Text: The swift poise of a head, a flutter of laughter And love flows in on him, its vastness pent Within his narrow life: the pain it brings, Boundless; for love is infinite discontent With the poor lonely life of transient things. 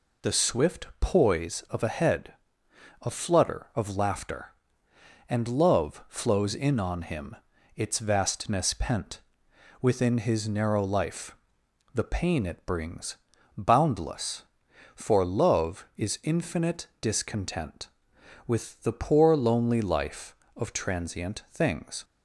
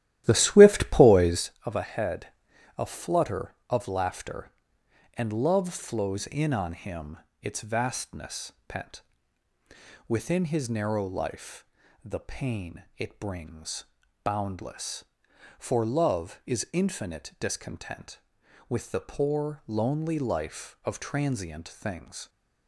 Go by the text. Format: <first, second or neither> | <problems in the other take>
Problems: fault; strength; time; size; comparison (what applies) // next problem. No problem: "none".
first | starts louder than the rest; strong; until 1.5 s; 13.5 dB // pauses between "vastness" and "pent"; slight; at 8.5 s; 0.16 s long // pauses between "pent" and "Within"; at 9.0 s; 1.0 s long; noticeable in the first